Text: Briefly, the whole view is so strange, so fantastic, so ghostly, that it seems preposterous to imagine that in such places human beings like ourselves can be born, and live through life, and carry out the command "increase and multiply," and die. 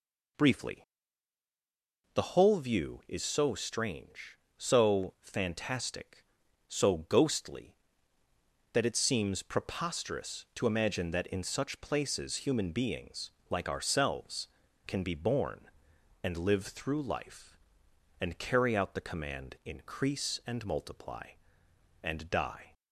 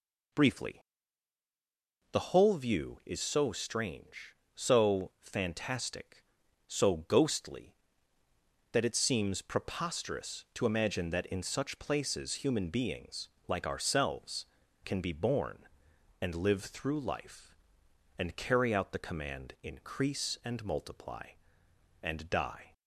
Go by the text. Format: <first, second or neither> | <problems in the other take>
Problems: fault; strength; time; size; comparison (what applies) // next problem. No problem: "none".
neither | pauses between "beings" and "like"; slight; the same in both